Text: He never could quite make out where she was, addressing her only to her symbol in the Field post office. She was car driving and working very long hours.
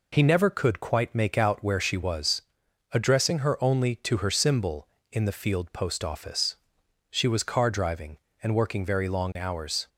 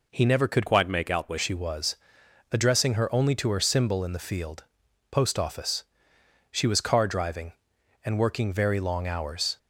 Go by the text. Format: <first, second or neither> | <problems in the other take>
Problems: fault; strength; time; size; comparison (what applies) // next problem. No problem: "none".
first | changes voice from "quite" to "where"; from 0.6 to 1.3 s; 0.7 s long // pauses between "Field" and "post"; noticeable; at 4.6 s; 0.46 s long